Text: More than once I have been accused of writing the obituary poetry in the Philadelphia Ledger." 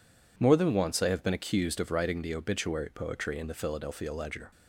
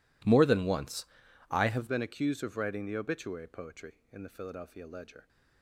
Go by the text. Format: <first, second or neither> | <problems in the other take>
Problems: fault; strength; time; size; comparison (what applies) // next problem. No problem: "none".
first | pauses between "once" and "I"; noticeable; at 1.0 s; 0.46 s long // changes voice at "been"; from 1.8 s on; 3.4 s long